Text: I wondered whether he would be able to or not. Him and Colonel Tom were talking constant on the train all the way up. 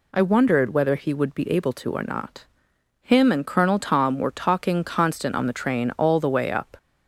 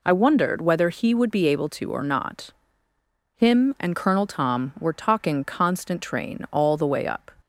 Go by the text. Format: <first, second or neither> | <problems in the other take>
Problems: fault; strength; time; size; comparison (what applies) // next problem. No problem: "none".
first | skips "on the"; at 6.0 s